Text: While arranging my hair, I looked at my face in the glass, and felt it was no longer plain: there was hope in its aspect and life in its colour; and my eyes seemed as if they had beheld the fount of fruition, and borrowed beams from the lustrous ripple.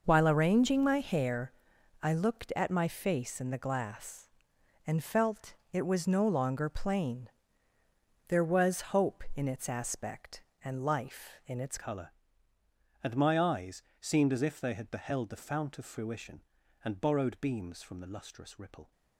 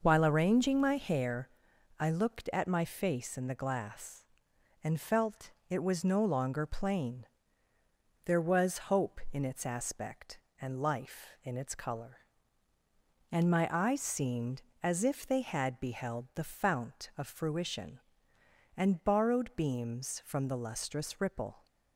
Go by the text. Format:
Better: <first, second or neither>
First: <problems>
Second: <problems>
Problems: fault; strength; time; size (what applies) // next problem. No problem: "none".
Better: second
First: starts louder than the rest; noticeable; until 1.0 s; 6 dB // pauses between "felt" and "it"; slight; at 5.5 s; 0.18 s long // changes voice at "colour"; from 11.7 s on; 7.2 s long // pauses between "eyes" and "seemed"; slight; at 13.8 s; 0.18 s long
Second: starts louder than the rest; noticeable; until 1.0 s; 6 dB // pauses between "felt" and "it"; slight; at 5.5 s; 0.18 s long